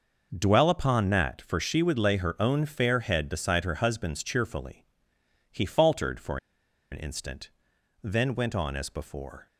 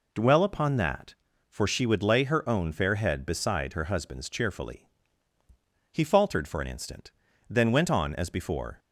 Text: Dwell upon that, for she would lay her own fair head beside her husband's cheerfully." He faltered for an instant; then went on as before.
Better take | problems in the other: second | pauses between "for" and "an"; noticeable; at 6.3 s; 0.53 s long

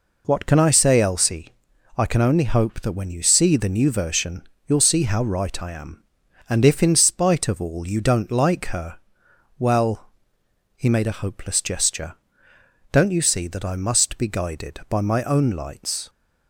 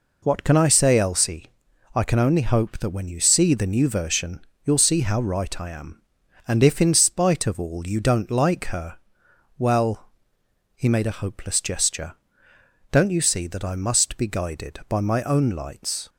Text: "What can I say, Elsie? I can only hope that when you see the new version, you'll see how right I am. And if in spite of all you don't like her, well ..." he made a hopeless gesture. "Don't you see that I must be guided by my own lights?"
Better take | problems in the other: neither | none

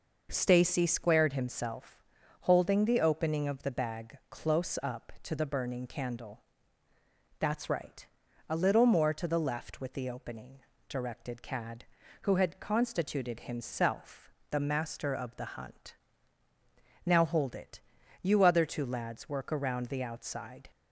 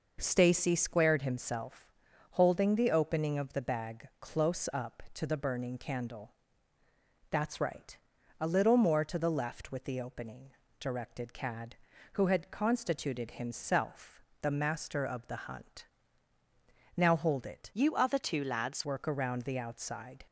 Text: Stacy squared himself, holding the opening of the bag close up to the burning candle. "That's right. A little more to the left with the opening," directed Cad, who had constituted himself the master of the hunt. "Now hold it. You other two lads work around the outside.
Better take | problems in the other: first | pauses between "himself" and "the"; slight; at 14.2 s; 0.20 s long; slight in the first // changes voice from "You" to "lads"; from 17.7 to 18.8 s; 1.1 s long

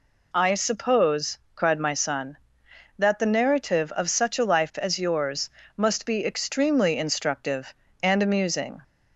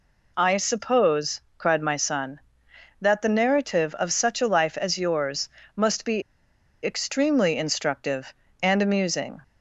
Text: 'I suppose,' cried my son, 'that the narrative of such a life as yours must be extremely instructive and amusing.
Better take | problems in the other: first | pauses between "yours" and "must"; slight; at 5.4 s; 0.28 s long; slight in the first // pauses between "be" and "extremely"; noticeable; at 6.2 s; 0.62 s long

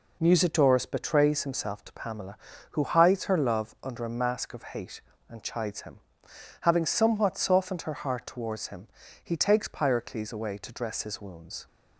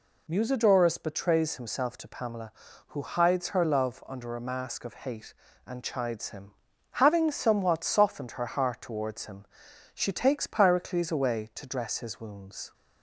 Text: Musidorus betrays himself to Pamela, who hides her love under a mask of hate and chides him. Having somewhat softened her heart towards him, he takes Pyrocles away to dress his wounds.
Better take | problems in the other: first | says "she" for "he"; at 9.9 s

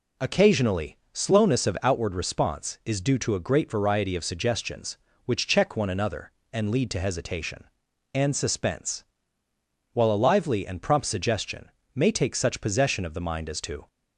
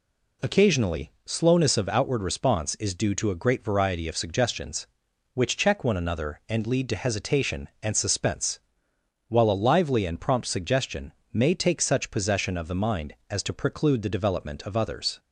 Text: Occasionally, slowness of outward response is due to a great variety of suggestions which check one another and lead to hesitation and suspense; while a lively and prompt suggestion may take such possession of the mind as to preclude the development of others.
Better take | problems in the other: second | pauses between "suggestion" and "may"; slight; at 11.6 s; 0.24 s long; slight in the second // stops before "preclude the development of others"; at 13.8 s

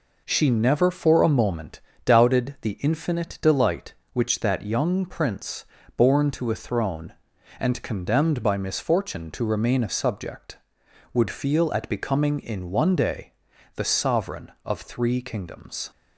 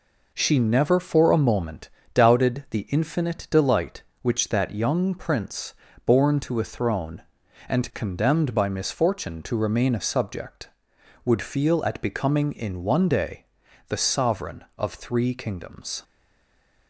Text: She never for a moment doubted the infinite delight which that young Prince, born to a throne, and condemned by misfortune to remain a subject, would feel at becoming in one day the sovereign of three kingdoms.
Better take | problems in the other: first | pauses between "moment" and "doubted"; slight; at 1.8 s; 0.26 s long; slight in the first // pauses between "day" and "the"; at 13.4 s; 0.44 s long; also in the first // stays silent after the last word; slight; from 16.0 s on; 0.8 s long

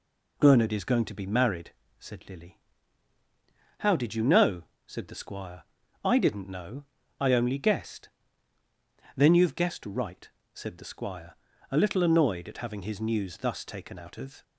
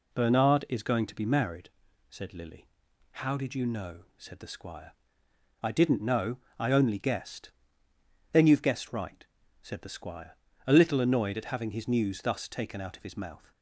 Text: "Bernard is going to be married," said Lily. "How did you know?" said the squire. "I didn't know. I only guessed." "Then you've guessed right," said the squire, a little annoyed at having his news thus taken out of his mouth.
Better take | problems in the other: second | stops before "his mouth"; at 14.4 s

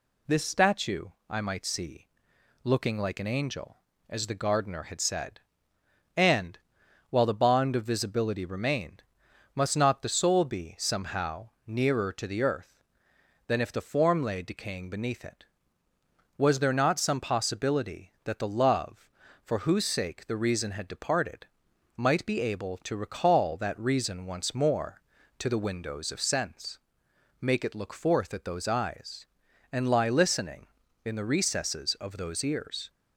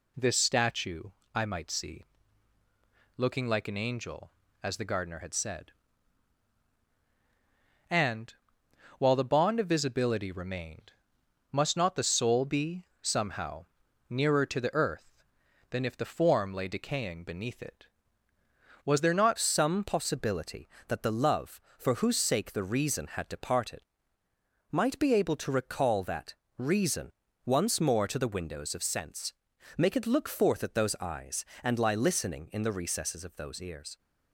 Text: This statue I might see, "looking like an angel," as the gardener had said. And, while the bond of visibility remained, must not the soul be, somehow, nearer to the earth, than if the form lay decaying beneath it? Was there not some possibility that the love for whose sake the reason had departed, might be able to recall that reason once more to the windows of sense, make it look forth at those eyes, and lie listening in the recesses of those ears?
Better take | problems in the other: first | pauses between "statue" and "I"; slight; at 1.0 s; 0.30 s long; slight in the first // changes voice at "some"; from 19.3 s on; 14.6 s long // pauses between "that" and "reason"; slight; at 26.3 s; 0.24 s long // pauses between "reason" and "once"; slight; at 27.1 s; 0.34 s long

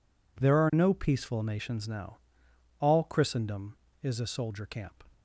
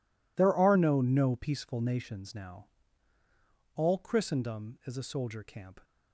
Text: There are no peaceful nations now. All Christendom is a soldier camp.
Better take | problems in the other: first | says "no" twice; at 1.0 s

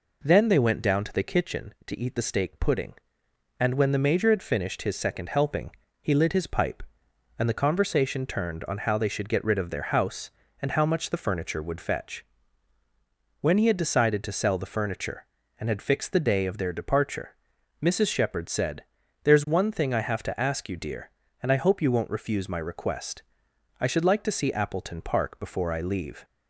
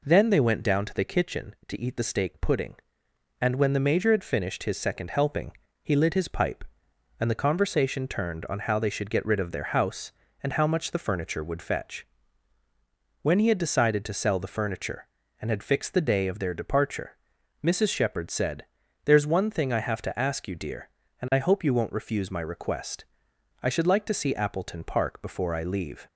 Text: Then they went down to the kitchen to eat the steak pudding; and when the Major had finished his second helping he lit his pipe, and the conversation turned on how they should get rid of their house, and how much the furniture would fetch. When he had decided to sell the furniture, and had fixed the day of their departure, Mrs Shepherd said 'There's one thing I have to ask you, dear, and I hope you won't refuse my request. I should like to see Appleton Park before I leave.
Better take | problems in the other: neither | pauses between "helping" and "he"; slight; the same in both // pauses between "said" and "There's"; the same in both

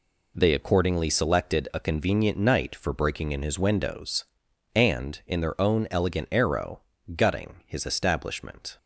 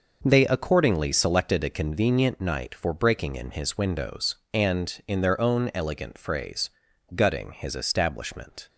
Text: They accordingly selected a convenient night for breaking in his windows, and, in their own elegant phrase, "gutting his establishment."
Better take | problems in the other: second | says "arrow" for "phrase"; at 6.2 s

